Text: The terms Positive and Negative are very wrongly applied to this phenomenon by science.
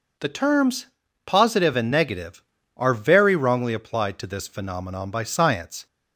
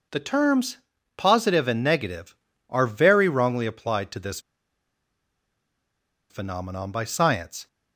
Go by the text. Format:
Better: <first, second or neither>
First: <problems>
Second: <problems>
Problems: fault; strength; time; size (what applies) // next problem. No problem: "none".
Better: first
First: pauses between "terms" and "Positive"; at 0.8 s; 0.40 s long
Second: pauses between "terms" and "Positive"; at 0.7 s; 0.40 s long // pauses between "this" and "phenomenon"; strong; at 4.3 s; 1.9 s long